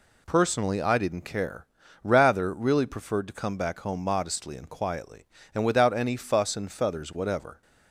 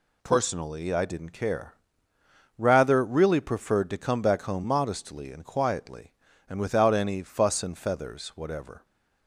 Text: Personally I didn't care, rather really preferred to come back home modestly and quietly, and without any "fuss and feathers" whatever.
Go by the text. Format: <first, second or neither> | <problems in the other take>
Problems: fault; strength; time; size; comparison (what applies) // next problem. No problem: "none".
neither | none